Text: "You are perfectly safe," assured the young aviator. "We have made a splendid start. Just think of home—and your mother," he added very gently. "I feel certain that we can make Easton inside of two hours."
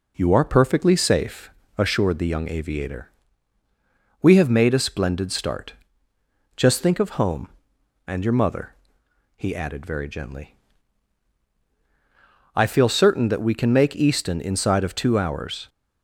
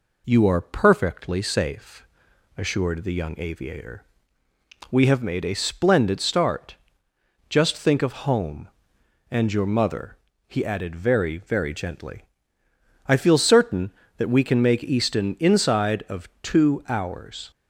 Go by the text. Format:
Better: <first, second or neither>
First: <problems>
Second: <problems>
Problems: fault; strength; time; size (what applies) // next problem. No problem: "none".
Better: first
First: none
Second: says "very" twice; at 11.3 s